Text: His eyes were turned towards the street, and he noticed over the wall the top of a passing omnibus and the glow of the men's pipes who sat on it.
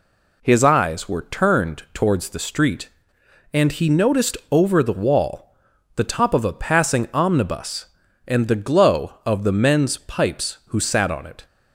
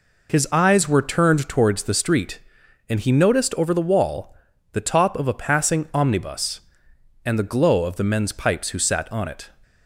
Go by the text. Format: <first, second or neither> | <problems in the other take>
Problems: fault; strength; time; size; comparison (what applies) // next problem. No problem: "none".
neither | pauses between "wall" and "the"; the same in both